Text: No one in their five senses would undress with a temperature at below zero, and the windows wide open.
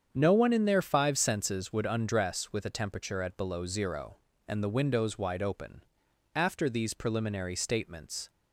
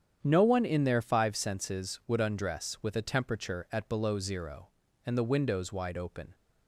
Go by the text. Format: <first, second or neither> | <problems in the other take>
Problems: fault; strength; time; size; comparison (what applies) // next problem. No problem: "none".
second | starts louder than the rest; strong; until 1.1 s; 7.5 dB; strong in the second // goes on to say "After these preliminary statements"; strong; from 6.3 s on; 1.9 s long